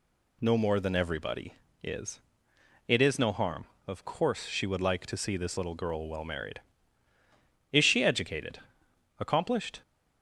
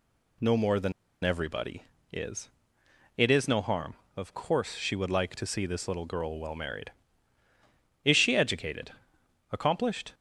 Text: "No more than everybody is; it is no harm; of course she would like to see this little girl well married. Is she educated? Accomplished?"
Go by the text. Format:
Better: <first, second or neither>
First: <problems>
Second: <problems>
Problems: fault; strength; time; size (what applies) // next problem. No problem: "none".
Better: first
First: none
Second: pauses between "than" and "everybody"; slight; at 0.9 s; 0.31 s long